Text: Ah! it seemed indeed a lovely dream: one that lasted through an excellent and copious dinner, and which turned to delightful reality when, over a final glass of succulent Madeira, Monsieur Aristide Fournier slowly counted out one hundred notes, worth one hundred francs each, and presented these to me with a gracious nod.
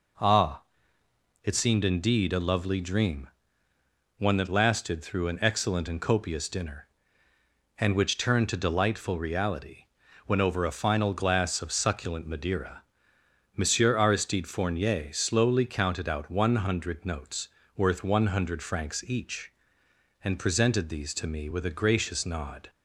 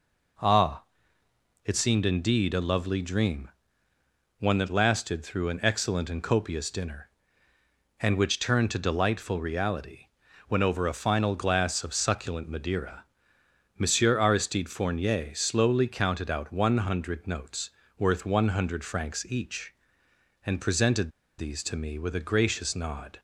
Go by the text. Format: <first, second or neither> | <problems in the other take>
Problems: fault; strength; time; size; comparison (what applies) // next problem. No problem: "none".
first | pauses between "reality" and "when"; at 10.0 s; 0.40 s long; also in the first // pauses between "presented" and "these"; slight; at 21.1 s; 0.28 s long